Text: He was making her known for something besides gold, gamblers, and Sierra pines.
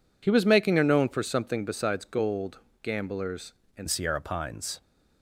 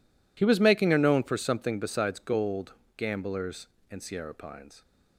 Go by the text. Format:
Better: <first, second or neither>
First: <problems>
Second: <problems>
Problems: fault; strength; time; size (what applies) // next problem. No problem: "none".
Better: second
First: changes voice at "Sierra"; from 3.8 s on; 1.0 s long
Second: none